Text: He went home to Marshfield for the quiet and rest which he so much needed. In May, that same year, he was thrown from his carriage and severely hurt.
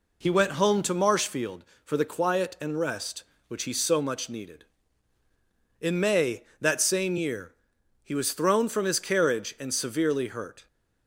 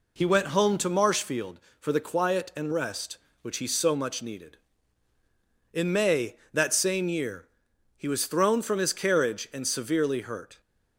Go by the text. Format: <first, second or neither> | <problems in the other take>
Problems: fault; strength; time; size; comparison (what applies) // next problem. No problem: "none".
neither | none